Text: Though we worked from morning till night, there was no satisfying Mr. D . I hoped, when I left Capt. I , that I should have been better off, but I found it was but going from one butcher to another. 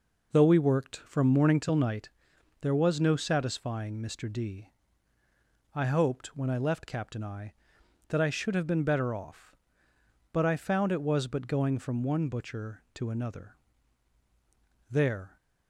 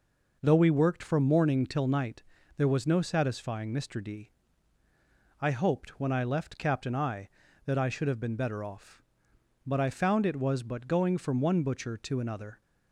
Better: second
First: goes on to say "There"; slight; from 14.8 s on; 0.48 s long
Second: none

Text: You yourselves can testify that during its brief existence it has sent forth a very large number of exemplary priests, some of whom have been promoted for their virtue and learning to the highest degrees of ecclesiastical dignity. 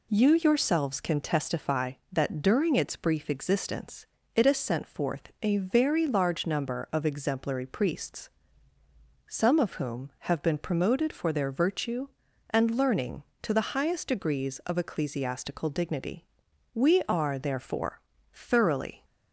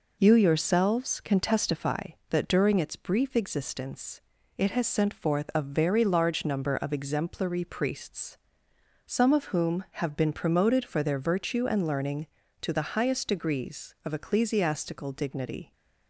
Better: second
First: pauses between "existence" and "it"; slight; at 4.0 s; 0.28 s long // goes on to say "We are therefore thoroughly"; strong; from 16.7 s on; 2.3 s long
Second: pauses between "existence" and "it"; at 4.1 s; 0.38 s long

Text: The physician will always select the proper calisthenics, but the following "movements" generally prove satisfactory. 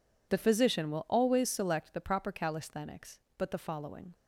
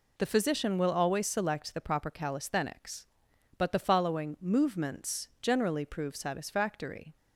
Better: second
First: stops before "movements generally prove satisfactory"; at 4.1 s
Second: none

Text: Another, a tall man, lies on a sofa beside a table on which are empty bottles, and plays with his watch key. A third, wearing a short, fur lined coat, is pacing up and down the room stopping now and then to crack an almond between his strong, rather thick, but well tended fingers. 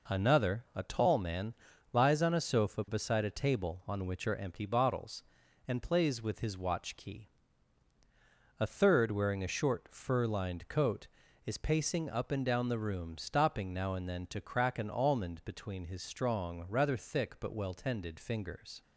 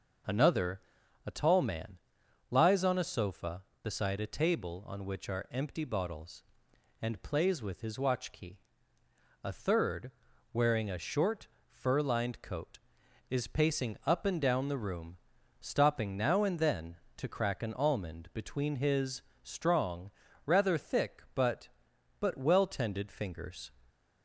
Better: first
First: none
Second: pauses between "room" and "stopping"; at 15.1 s; 0.42 s long // pauses between "his" and "strong"; slight; at 19.2 s; 0.18 s long // says "but" twice; at 22.2 s

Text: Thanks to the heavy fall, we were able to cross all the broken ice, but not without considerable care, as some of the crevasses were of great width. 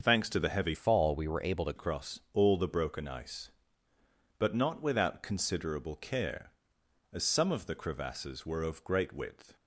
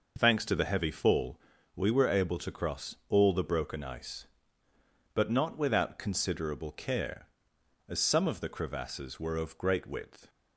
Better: second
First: starts louder than the rest; until 1.0 s; 6.5 dB // changes voice from "fall" to "to"; from 0.7 to 1.7 s; 1.0 s long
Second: none

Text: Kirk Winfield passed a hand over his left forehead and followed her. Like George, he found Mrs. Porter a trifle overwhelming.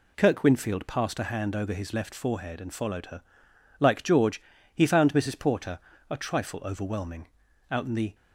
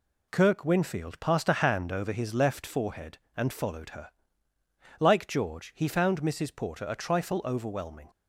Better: second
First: pauses between "Porter" and "a"; slight; at 5.7 s; 0.30 s long // goes on to say "Out in the"; slight; from 7.7 s on; 0.44 s long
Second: none

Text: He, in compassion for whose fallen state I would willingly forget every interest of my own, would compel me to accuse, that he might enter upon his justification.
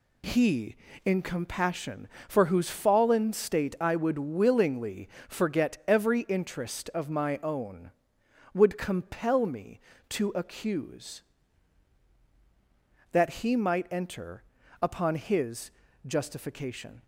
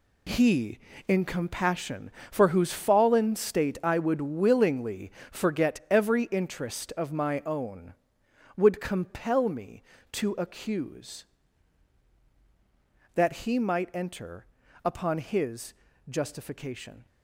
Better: first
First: pauses between "willingly" and "forget"; slight; at 5.0 s; 0.22 s long // pauses between "enter" and "upon"; at 14.4 s; 0.40 s long // pauses between "his" and "justification"; at 15.6 s; 0.38 s long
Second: gets quieter; strong; throughout; 10 dB // pauses between "willingly" and "forget"; slight; at 5.0 s; 0.22 s long // pauses between "enter" and "upon"; at 14.4 s; 0.40 s long // pauses between "his" and "justification"; at 15.7 s; 0.38 s long

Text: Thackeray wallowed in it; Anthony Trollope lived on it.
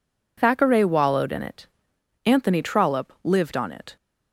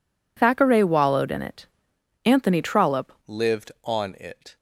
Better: first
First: none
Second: changes voice at "lived"; from 3.2 s on; 1.3 s long

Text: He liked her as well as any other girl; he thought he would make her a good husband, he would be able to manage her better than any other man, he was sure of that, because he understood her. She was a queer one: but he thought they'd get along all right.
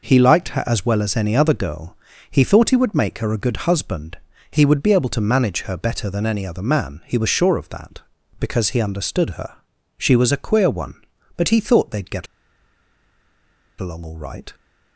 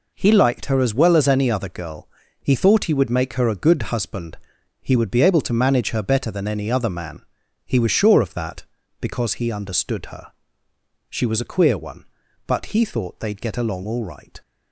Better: second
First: pauses between "get" and "along"; strong; at 12.2 s; 1.5 s long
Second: none

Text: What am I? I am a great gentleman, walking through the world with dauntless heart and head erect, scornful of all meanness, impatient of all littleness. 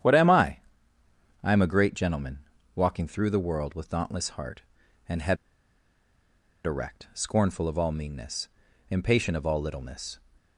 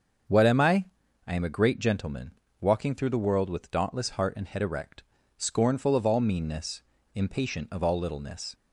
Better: second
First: starts louder than the rest; strong; until 1.8 s; 10 dB // pauses between "head" and "erect"; strong; at 5.3 s; 1.2 s long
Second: starts louder than the rest; until 1.7 s; 7 dB

